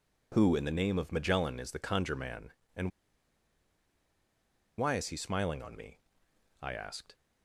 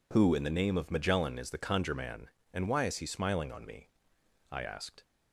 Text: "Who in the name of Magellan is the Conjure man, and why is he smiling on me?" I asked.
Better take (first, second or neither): second